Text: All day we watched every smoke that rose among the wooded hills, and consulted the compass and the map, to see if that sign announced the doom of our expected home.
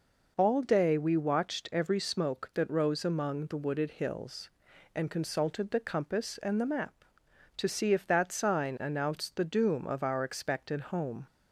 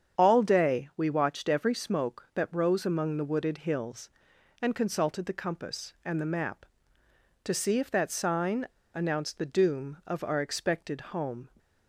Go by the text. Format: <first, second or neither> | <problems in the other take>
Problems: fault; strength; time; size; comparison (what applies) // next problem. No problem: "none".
first | starts louder than the rest; strong; until 1.2 s; 8 dB // pauses between "sign" and "announced"; slight; at 8.6 s; 0.26 s long